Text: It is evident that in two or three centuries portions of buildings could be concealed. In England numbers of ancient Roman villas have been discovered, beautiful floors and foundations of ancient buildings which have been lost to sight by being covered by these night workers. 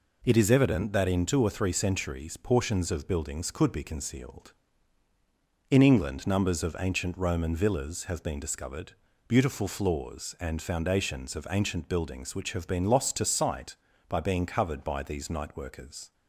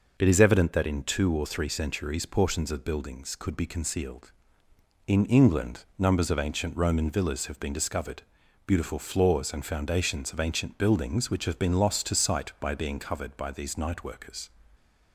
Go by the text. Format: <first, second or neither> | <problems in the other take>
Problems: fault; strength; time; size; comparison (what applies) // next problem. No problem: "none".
neither | none